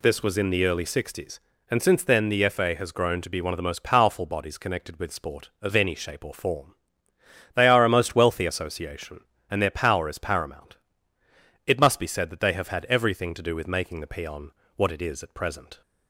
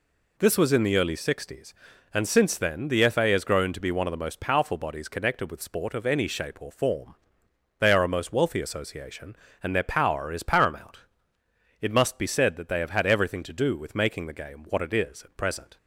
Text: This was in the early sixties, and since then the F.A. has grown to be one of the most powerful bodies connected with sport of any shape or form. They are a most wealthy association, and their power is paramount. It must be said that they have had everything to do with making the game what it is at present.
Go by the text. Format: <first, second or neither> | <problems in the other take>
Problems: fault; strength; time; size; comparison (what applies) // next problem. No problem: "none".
second | says "peon" for "game"; at 14.0 s